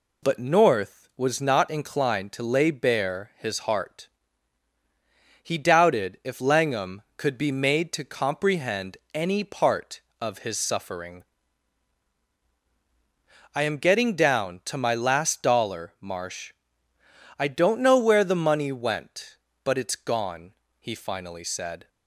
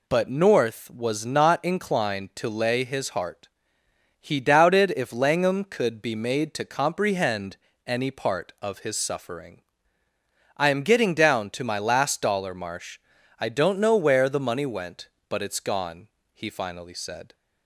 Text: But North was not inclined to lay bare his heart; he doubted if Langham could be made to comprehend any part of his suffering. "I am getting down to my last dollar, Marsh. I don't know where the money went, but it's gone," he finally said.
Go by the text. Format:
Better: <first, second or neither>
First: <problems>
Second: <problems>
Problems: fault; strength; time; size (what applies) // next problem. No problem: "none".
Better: first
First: none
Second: skips "bare"; at 2.8 s // pauses between "comprehend" and "any"; slight; at 7.5 s; 0.28 s long